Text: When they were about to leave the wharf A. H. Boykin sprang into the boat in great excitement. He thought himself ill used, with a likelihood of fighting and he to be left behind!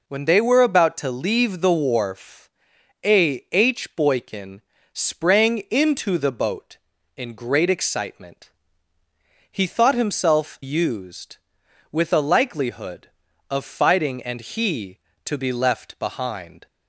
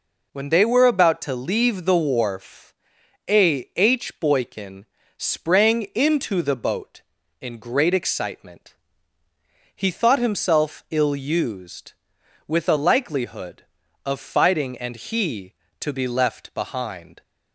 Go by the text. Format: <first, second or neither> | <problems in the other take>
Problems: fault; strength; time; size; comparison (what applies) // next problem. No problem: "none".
second | pauses between "wharf" and "A"; noticeable; at 2.4 s; 0.56 s long; noticeable in the second // pauses between "Boykin" and "sprang"; slight; at 4.5 s; 0.32 s long; slight in the second // skips "ill"; at 10.6 s